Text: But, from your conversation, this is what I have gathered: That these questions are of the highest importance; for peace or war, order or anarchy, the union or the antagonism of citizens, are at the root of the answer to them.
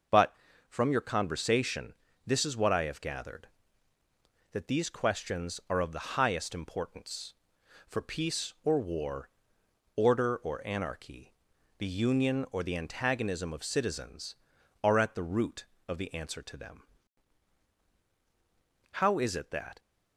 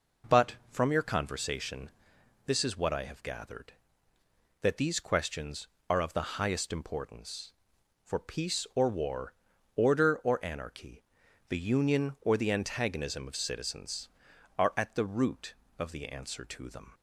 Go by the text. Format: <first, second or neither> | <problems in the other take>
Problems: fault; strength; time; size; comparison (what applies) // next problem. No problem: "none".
second | goes on to say "How is it that"; noticeable; from 18.9 s on; 0.86 s long